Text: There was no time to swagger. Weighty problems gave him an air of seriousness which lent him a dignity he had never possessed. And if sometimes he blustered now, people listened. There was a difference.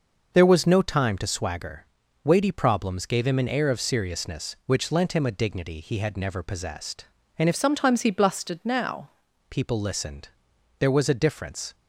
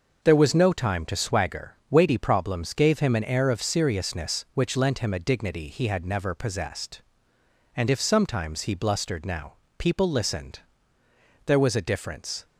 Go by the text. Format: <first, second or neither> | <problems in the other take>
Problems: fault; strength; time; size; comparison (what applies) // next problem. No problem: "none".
second | changes voice from "sometimes" to "now"; from 7.5 to 9.0 s; 1.5 s long